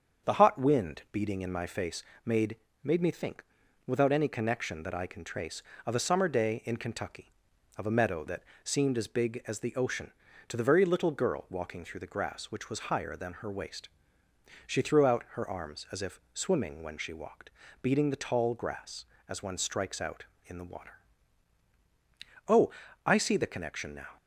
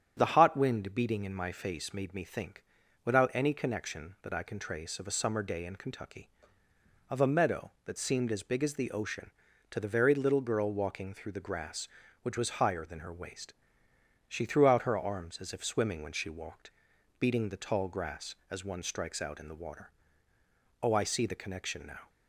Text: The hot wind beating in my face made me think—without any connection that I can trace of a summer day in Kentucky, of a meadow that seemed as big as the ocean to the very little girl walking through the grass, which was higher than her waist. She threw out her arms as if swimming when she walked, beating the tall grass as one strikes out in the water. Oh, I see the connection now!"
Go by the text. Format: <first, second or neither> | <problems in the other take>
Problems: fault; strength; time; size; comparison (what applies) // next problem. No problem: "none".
second | starts louder than the rest; strong; until 1.3 s; 7.5 dB; strong in the second // pauses between "face" and "made"; slight; at 2.0 s; 0.22 s long // says "made" twice; at 2.8 s // pauses between "that" and "seemed"; slight; at 8.4 s; 0.20 s long